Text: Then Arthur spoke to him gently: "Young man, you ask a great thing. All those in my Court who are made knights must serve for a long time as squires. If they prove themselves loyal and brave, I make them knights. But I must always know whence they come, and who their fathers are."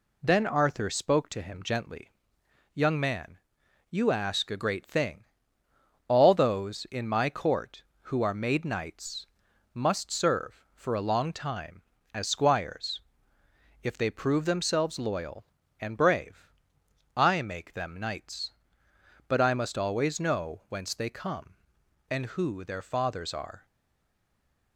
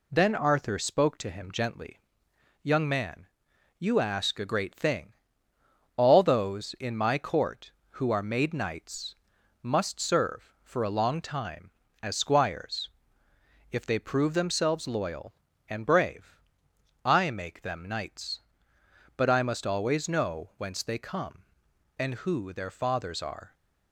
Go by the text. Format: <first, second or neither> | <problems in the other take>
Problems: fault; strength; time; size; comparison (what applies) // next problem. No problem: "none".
second | pauses between "knights" and "must"; noticeable; at 9.2 s; 0.48 s long; noticeable in the second // stays silent after the last word; from 23.6 s on; 1.1 s long